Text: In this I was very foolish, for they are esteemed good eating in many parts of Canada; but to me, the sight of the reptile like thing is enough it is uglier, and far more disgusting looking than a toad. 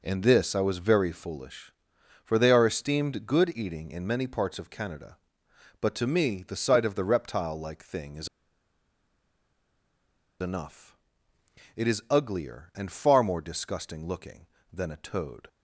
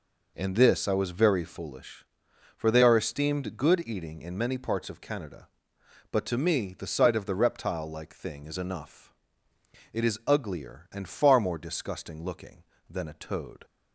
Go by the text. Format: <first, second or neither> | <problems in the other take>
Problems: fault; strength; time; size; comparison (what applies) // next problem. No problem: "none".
second | pauses between "is" and "enough"; strong; at 8.2 s; 2.1 s long // pauses between "enough" and "it"; noticeable; at 10.9 s; 0.82 s long; noticeable in the second